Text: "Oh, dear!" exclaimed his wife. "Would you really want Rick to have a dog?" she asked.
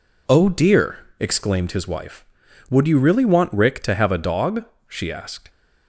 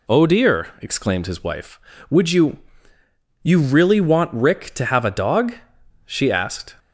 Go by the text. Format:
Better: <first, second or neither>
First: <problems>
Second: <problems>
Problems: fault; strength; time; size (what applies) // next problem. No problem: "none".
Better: first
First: none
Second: says "you" twice; at 3.4 s